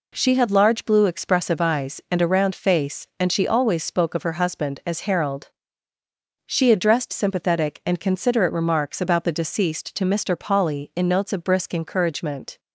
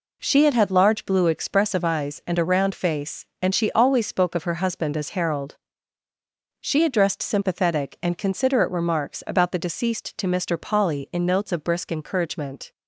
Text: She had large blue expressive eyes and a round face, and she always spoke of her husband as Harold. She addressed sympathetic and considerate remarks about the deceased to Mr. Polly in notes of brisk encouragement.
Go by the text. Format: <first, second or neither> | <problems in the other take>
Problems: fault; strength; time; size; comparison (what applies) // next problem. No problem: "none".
first | says "had" twice; at 0.5 s